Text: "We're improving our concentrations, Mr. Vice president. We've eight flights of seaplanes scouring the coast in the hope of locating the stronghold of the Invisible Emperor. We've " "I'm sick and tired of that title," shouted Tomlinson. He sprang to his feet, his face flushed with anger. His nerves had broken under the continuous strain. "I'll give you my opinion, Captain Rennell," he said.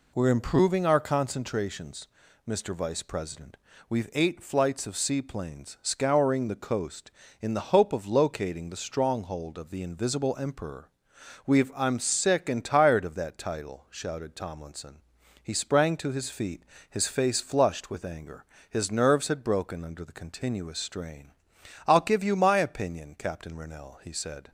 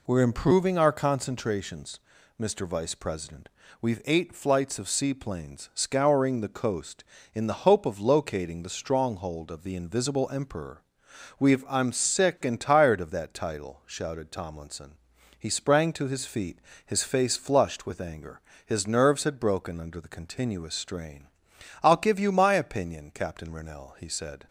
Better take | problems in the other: neither | none

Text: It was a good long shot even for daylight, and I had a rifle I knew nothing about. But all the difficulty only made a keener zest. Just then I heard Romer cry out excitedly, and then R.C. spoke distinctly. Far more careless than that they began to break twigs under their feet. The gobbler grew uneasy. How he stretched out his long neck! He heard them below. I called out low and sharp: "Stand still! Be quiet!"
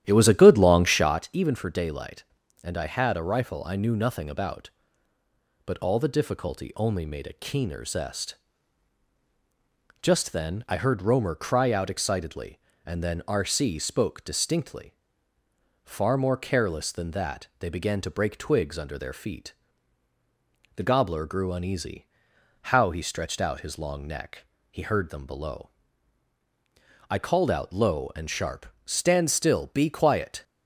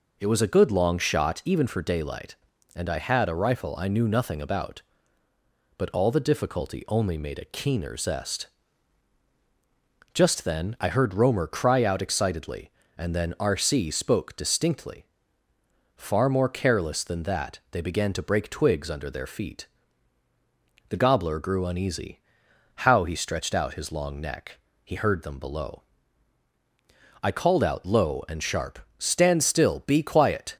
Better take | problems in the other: second | starts louder than the rest; strong; until 1.2 s; 11.5 dB

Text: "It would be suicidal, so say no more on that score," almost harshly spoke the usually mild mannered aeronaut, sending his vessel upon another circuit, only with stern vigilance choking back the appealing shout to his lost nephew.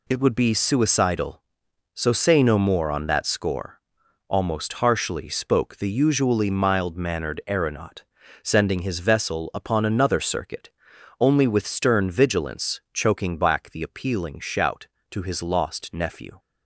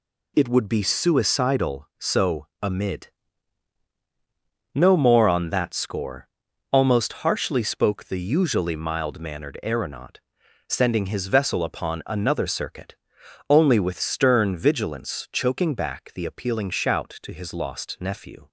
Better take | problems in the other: first | says "amid" for "say"; at 2.6 s

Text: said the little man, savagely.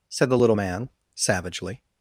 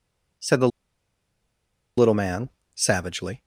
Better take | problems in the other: first | pauses between "the" and "little"; strong; at 0.6 s; 1.2 s long

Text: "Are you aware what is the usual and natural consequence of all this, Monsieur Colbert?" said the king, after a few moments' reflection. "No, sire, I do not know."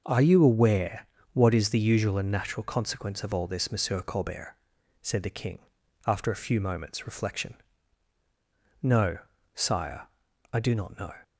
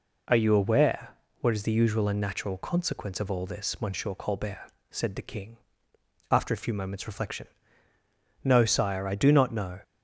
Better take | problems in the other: neither | pauses between "aware" and "what"; slight; the same in both

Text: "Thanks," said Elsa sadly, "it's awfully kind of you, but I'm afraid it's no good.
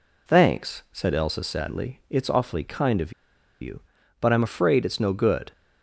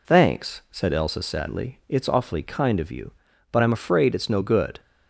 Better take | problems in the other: second | pauses between "of" and "you"; noticeable; at 3.1 s; 0.49 s long

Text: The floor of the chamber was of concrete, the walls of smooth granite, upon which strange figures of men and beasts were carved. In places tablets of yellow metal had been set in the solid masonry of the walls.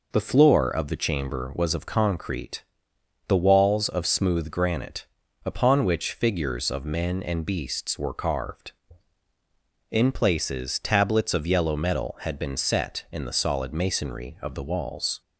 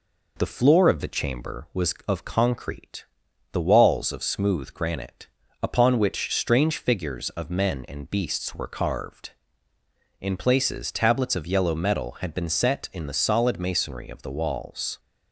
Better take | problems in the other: second | skips "strange"; at 6.1 s

